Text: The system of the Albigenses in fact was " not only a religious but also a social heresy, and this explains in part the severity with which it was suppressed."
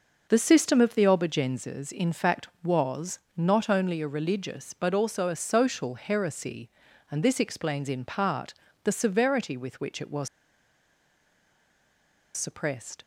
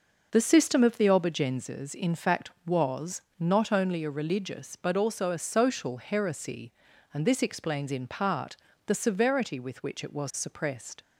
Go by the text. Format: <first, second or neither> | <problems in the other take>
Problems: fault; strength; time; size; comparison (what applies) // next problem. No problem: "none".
second | pauses between "part" and "the"; slight; at 8.5 s; 0.30 s long; slight in the second // pauses between "was" and "suppressed"; strong; at 10.2 s; 2.0 s long